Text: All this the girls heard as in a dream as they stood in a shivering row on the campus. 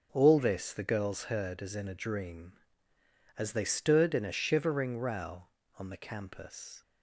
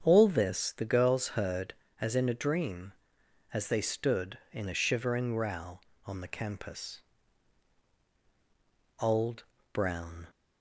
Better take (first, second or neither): first